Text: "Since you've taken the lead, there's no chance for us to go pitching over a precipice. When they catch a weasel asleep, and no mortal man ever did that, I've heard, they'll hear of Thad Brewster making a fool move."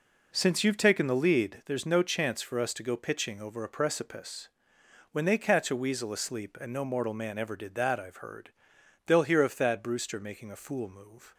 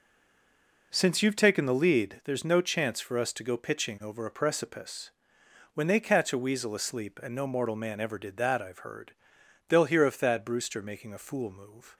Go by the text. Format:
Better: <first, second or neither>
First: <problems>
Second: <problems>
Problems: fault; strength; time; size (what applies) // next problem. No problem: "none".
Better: first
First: none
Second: stays silent before the first word; slight; until 0.9 s; 0.9 s long